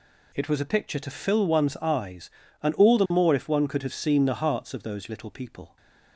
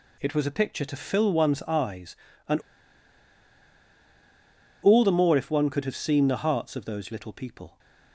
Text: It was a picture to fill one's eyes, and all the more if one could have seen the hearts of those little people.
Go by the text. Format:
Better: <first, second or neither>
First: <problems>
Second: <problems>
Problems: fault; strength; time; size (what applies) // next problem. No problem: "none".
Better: first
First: none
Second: pauses between "and" and "all"; strong; at 2.5 s; 2.2 s long